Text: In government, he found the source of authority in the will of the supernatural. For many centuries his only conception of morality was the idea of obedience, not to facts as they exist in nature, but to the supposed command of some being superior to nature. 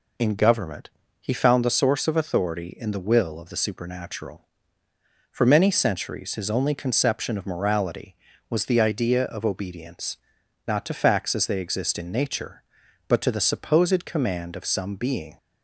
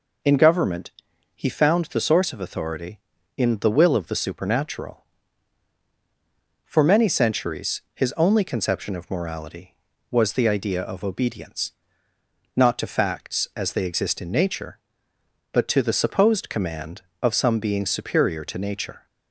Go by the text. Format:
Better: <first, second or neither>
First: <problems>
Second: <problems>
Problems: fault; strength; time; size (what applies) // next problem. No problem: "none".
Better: second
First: stops before "superior to nature"; at 15.3 s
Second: none